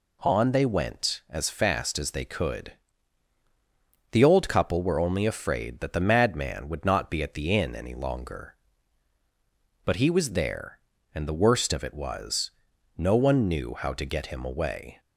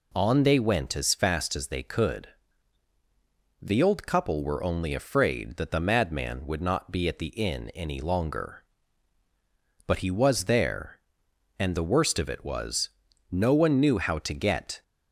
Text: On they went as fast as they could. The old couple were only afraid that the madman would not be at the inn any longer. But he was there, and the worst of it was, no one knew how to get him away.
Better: first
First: none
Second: stops before "him away"; at 14.8 s

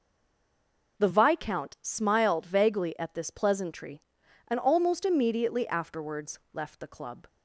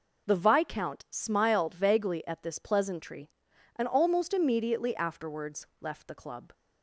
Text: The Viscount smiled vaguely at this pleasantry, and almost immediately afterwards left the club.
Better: second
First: stays silent before the first word; until 0.9 s; 0.9 s long // pauses between "afterwards" and "left"; slight; at 6.3 s; 0.16 s long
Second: pauses between "afterwards" and "left"; slight; at 5.6 s; 0.16 s long

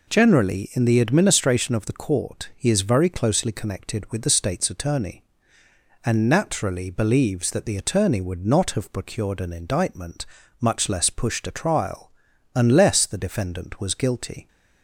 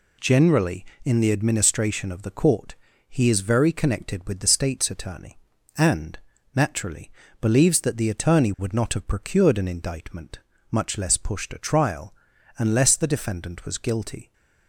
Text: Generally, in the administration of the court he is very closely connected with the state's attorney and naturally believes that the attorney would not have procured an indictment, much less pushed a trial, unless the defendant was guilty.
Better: first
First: none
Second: pauses between "court" and "he"; slight; at 2.7 s; 0.36 s long // skips "closely"; at 3.7 s // pauses between "and" and "naturally"; slight; at 6.1 s; 0.36 s long // pauses between "naturally" and "believes"; slight; at 7.1 s; 0.30 s long

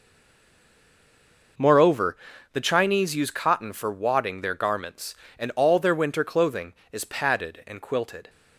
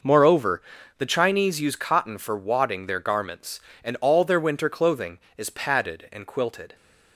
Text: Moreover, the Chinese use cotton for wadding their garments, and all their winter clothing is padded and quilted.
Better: second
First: stays silent before the first word; noticeable; until 1.5 s; 1.5 s long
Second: none

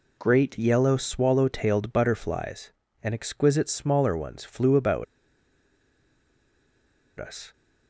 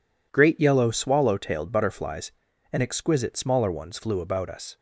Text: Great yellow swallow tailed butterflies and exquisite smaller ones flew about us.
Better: second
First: pauses between "about" and "us"; strong; at 5.0 s; 2.1 s long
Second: none

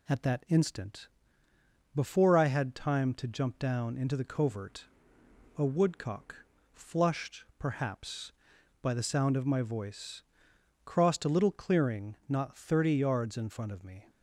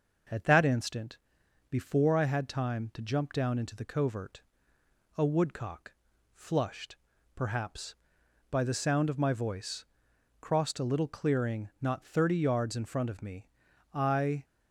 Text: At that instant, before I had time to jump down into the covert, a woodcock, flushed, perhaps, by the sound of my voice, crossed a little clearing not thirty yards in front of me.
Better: first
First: none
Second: goes on to say "I"; from 13.9 s on; 0.50 s long

